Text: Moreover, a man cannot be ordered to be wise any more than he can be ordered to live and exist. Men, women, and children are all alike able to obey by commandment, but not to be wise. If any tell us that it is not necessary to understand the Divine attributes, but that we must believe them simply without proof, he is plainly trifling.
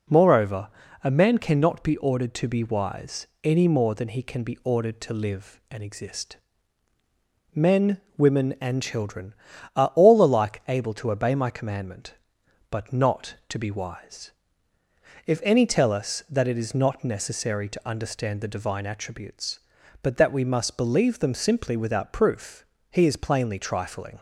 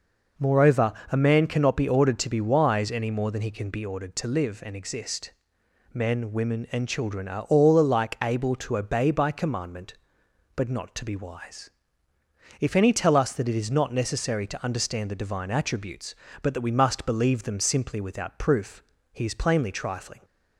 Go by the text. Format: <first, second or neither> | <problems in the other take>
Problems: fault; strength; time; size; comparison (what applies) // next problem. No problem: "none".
second | pauses between "wise" and "any"; slight; at 3.2 s; 0.18 s long // says "my" for "by"; at 11.3 s